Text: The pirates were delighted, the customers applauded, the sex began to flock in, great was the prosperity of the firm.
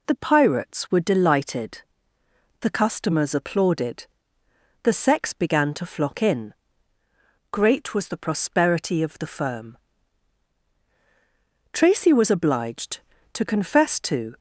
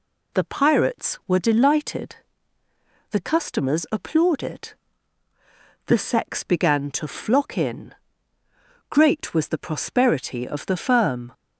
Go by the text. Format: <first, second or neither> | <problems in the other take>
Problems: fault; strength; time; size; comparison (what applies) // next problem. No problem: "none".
second | goes on to say "Tracy was obliged to confess to"; strong; from 11.7 s on; 2.6 s long